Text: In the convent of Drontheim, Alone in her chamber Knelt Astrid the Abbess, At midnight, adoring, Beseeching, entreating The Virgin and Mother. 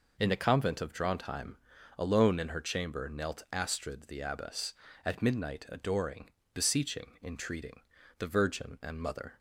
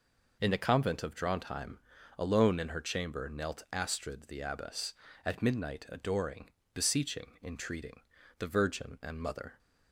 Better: neither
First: pauses between "entreating" and "The"; at 7.8 s; 0.38 s long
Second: pauses between "entreating" and "The"; at 8.0 s; 0.38 s long

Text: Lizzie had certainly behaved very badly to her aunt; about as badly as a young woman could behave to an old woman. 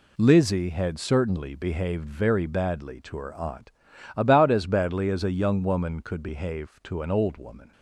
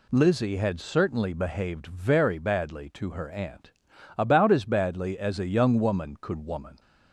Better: first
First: none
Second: skips "behave to an old"; at 6.4 s

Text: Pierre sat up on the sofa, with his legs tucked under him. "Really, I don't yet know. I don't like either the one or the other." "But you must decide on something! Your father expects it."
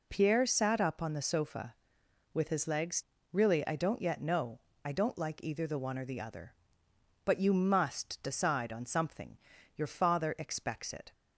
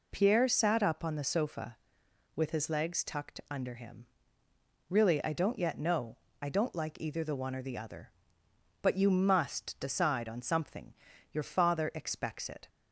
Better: second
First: skips "tucked under him"; at 3.1 s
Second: none

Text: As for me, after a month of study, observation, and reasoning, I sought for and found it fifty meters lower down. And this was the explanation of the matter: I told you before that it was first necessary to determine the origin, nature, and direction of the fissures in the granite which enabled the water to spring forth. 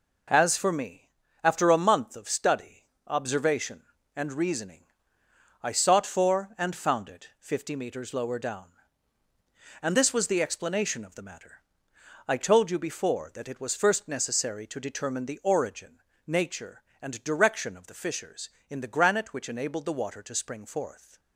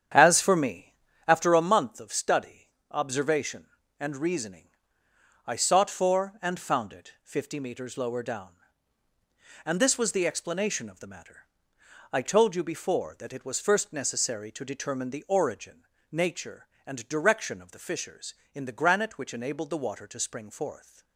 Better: first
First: none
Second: starts louder than the rest; strong; until 1.5 s; 8.5 dB

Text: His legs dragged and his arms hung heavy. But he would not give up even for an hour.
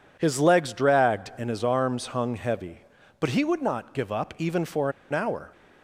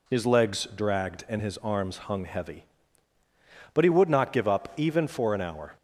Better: second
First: pauses between "for" and "an"; slight; at 4.9 s; 0.19 s long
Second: none

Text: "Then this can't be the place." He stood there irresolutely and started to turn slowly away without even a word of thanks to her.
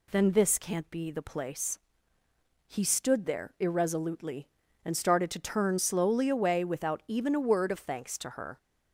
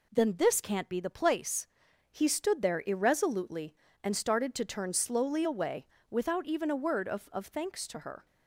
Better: first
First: none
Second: pauses between "away" and "without"; slight; at 5.8 s; 0.24 s long // says "of" twice; at 7.3 s

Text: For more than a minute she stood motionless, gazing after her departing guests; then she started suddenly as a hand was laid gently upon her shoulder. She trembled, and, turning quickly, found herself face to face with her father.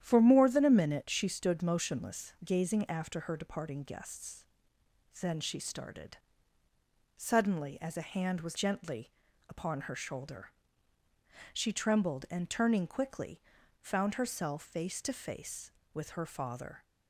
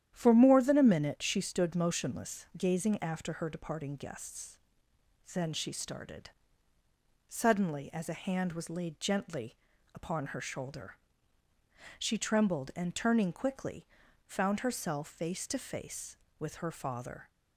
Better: second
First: starts louder than the rest; strong; until 1.0 s; 10 dB // pauses between "started" and "suddenly"; noticeable; at 6.1 s; 0.98 s long // skips "laid"; at 8.5 s // pauses between "gently" and "upon"; at 9.1 s; 0.38 s long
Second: starts louder than the rest; strong; until 1.1 s; 10.5 dB // pauses between "started" and "suddenly"; noticeable; at 6.3 s; 0.97 s long // pauses between "gently" and "upon"; at 9.5 s; 0.38 s long

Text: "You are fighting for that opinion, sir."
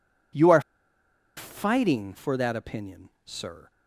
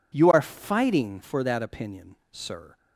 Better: second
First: pauses between "are" and "fighting"; noticeable; at 0.5 s; 0.77 s long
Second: none

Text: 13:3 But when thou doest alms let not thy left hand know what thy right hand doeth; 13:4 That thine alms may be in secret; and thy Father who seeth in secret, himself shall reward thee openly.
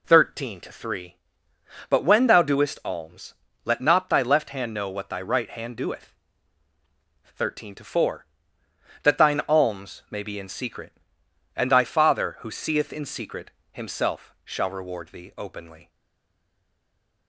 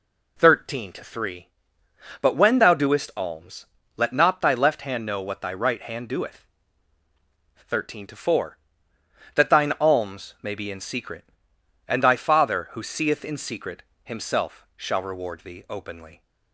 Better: second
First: pauses between "alms" and "let"; slight; at 3.3 s; 0.30 s long // stays silent after the last word; noticeable; from 15.8 s on; 1.4 s long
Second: pauses between "alms" and "let"; slight; at 3.6 s; 0.30 s long

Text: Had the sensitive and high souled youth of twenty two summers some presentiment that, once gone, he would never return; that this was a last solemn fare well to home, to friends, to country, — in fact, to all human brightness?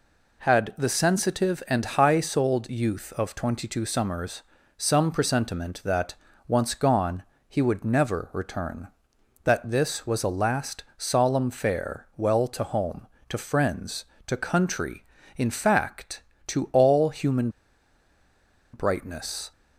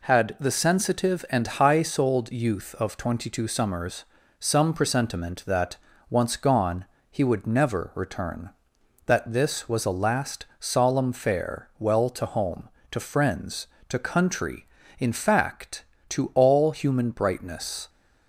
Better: second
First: pauses between "summers" and "some"; slight; at 4.4 s; 0.36 s long // pauses between "human" and "brightness"; at 17.4 s; 1.2 s long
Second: pauses between "summers" and "some"; slight; at 4.0 s; 0.36 s long

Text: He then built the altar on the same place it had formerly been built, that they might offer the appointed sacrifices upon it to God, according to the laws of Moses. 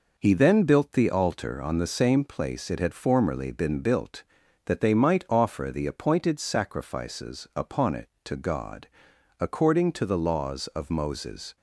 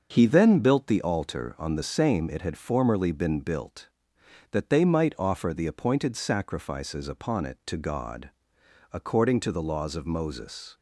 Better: first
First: none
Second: starts louder than the rest; until 1.1 s; 6 dB // skips "place"; at 2.2 s

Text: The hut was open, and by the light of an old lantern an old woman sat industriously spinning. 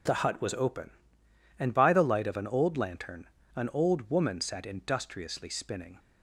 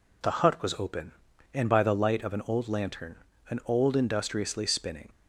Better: first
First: pauses between "lantern" and "an"; slight; at 3.2 s; 0.30 s long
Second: pauses between "lantern" and "an"; slight; at 3.1 s; 0.34 s long // skips "woman sat"; at 3.9 s

